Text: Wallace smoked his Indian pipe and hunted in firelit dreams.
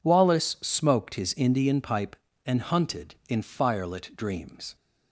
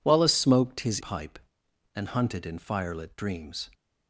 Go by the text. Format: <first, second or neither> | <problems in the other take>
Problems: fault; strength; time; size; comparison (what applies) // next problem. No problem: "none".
first | skips "Indian"; at 0.9 s